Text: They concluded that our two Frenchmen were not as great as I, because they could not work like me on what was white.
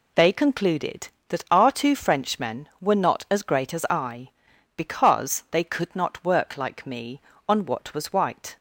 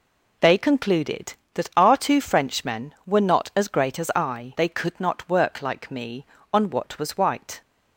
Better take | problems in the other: first | skips "because"; at 4.5 s

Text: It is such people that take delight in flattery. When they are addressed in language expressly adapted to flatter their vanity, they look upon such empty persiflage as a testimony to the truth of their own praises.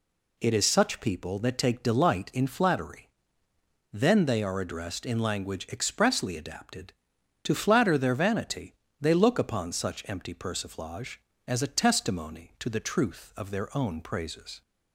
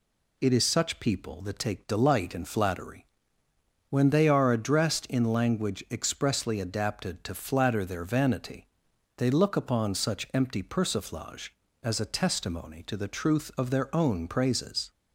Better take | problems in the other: second | says "Then" for "When"; at 3.9 s

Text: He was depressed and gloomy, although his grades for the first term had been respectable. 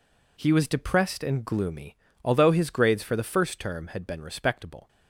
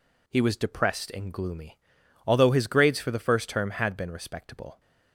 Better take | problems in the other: neither | none

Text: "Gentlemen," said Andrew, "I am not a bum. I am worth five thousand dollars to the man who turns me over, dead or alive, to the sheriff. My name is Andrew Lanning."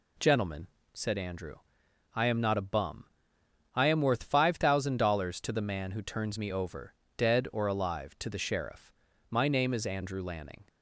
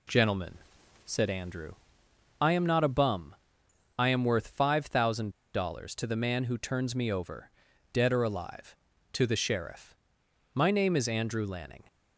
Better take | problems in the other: first | pauses between "thousand" and "dollars"; slight; at 5.3 s; 0.23 s long

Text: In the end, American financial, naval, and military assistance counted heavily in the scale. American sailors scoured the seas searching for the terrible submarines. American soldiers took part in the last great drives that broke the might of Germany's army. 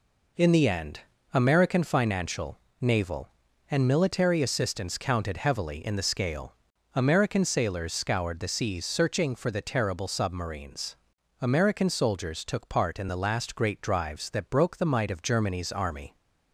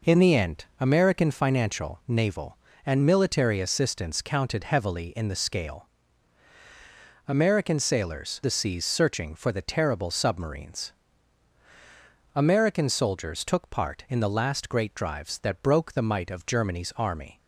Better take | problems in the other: first | skips "scoured"; at 8.4 s

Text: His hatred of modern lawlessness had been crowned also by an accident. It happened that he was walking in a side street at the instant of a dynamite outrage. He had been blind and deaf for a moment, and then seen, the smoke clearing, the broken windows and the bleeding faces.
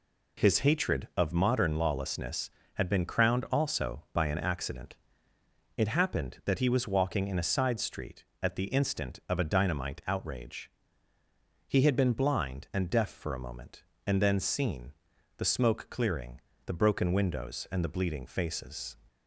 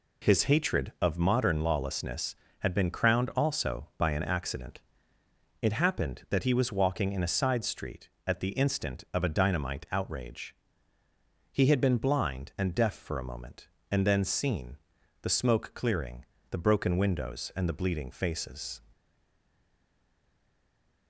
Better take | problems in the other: first | stays silent after the last word; from 18.9 s on; 2.1 s long

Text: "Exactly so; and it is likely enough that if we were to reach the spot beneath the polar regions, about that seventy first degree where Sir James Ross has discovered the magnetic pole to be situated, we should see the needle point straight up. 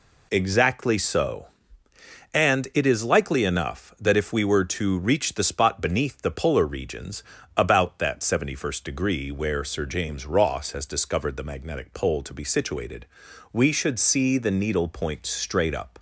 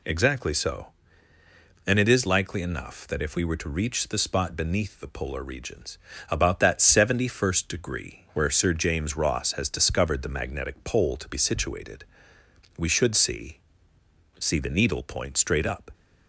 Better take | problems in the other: first | says "see" twice; at 14.3 s

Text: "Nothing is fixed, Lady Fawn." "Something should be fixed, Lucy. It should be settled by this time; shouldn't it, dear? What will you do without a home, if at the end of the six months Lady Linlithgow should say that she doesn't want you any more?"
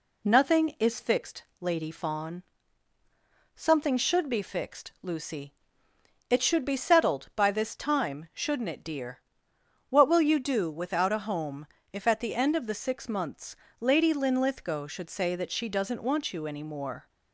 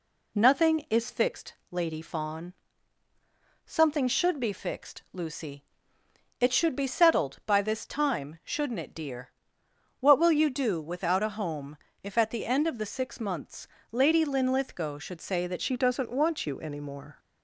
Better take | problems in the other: first | pauses between "months" and "Lady"; slight; at 13.6 s; 0.24 s long; slight in the first // changes voice at "she"; from 15.6 s on; 1.5 s long

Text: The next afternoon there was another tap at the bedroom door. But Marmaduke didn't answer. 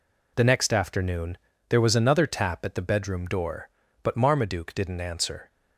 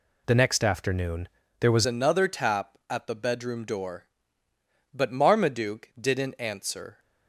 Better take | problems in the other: first | pauses between "afternoon" and "there"; slight; at 1.2 s; 0.30 s long; slight in the first // changes voice at "another"; from 1.8 s on; 5.1 s long

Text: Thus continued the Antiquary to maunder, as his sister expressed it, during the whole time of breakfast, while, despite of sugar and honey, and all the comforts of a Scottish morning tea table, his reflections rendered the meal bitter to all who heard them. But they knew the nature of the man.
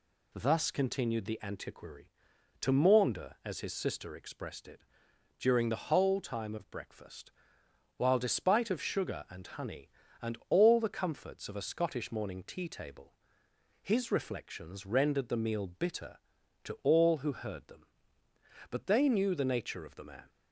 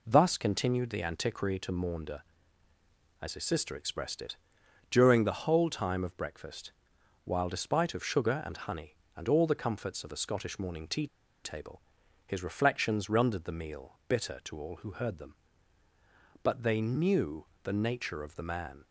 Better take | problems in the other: first | pauses between "tea" and "table"; at 11.0 s; 0.37 s long // pauses between "knew" and "the"; slight; at 17.4 s; 0.18 s long

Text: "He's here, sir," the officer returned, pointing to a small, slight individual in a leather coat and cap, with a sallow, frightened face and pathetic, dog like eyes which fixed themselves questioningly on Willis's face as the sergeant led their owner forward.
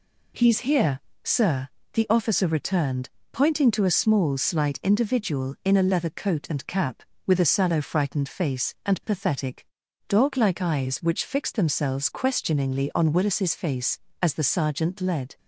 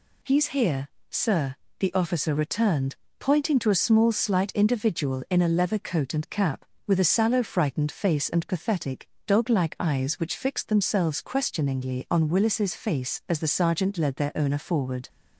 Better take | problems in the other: second | stops before "their owner forward"; at 15.3 s

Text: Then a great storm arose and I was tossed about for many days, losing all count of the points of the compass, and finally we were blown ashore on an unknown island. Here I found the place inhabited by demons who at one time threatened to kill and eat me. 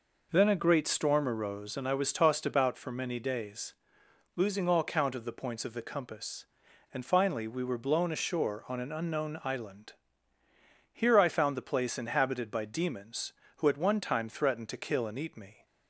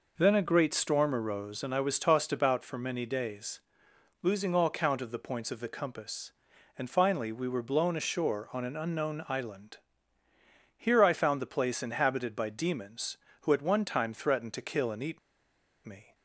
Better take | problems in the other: first | pauses between "eat" and "me"; noticeable; at 15.1 s; 0.67 s long

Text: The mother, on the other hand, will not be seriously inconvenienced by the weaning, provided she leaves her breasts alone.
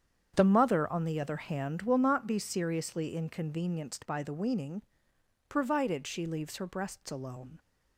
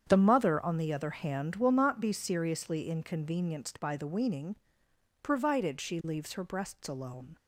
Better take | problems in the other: neither | starts louder than the rest; strong; the same in both

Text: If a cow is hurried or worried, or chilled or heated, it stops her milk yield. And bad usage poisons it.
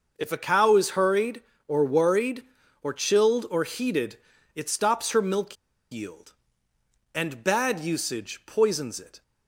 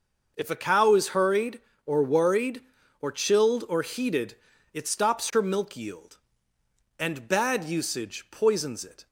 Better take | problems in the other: second | pauses between "milk" and "yield"; at 5.5 s; 0.36 s long

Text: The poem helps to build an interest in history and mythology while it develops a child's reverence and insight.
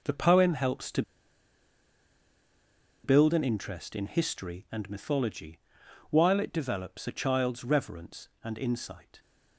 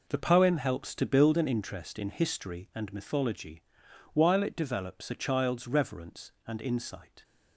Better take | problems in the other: second | pauses between "to" and "build"; strong; at 1.0 s; 2.0 s long // pauses between "mythology" and "while"; noticeable; at 5.5 s; 0.50 s long; noticeable in the second

